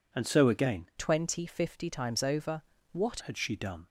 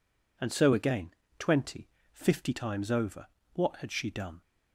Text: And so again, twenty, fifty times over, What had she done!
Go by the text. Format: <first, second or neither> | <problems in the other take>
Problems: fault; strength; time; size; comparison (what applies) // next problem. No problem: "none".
second | changes voice from "twenty" to "What"; from 0.9 to 3.1 s; 2.2 s long